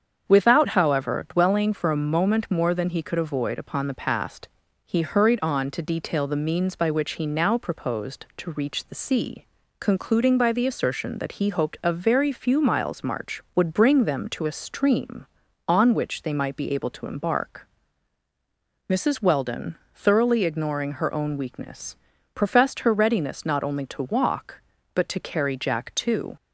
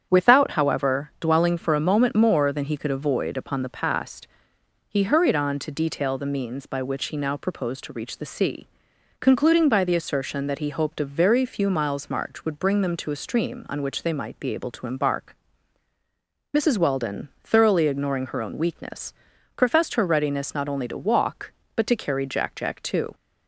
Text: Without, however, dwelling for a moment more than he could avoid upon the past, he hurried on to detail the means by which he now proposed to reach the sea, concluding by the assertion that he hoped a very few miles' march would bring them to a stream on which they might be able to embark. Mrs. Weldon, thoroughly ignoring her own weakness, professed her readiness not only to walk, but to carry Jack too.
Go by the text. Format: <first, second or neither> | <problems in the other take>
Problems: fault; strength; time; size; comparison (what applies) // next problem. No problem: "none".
first | starts louder than the rest; strong; until 1.1 s; 8.5 dB; strong in the first // says "Jack" twice; at 22.5 s